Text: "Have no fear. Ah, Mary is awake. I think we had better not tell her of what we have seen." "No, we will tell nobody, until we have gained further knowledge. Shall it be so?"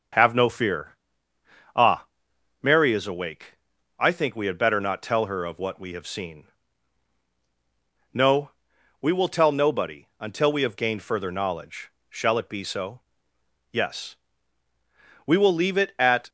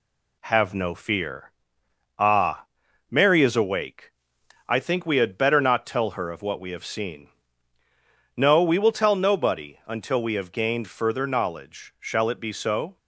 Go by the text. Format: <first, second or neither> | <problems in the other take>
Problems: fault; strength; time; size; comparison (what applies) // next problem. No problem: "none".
second | starts louder than the rest; noticeable; until 1.9 s; 6 dB // goes on to say "Yes We will leave it at"; strong; from 13.7 s on; 2.5 s long